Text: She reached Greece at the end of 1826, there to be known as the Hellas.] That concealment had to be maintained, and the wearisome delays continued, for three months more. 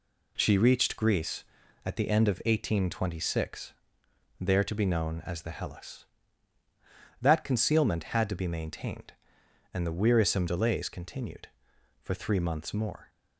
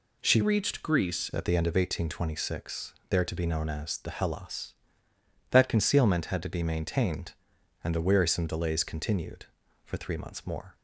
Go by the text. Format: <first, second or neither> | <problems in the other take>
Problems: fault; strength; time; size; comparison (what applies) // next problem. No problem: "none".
first | changes voice from "reached" to "Greece"; from 0.4 to 1.2 s; 0.8 s long